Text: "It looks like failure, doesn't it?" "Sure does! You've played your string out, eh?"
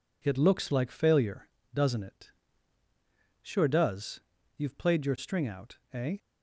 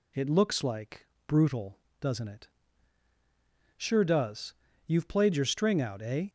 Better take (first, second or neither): first